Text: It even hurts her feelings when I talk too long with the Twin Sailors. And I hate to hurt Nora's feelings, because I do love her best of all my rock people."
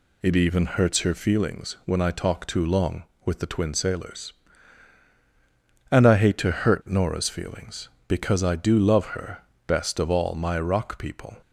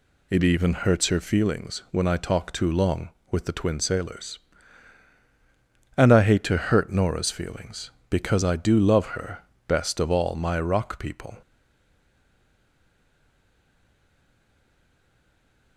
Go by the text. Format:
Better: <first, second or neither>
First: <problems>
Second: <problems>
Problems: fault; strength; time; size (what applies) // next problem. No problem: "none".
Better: first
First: pauses between "her" and "best"; slight; at 9.3 s; 0.28 s long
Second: pauses between "her" and "best"; slight; at 9.3 s; 0.28 s long // stays silent after the last word; strong; from 11.4 s on; 4.3 s long